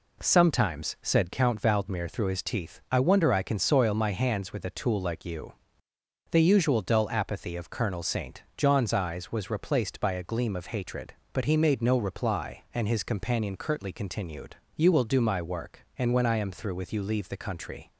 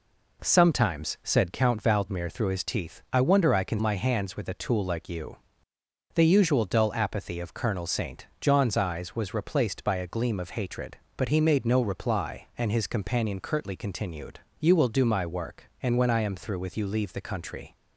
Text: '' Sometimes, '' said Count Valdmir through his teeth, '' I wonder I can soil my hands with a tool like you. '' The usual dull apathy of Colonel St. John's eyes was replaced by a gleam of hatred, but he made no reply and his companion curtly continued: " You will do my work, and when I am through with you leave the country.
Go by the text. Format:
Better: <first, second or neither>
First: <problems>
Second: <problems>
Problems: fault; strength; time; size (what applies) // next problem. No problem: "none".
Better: first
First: none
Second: skips "soil"; at 3.7 s